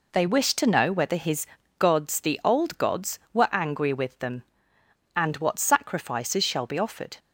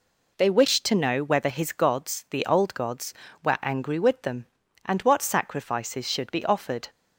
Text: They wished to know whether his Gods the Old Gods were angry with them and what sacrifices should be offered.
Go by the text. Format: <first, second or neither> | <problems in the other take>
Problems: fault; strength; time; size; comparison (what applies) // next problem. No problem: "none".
second | pauses between "his" and "Gods"; slight; at 1.4 s; 0.32 s long // says "shall" for "should"; at 6.4 s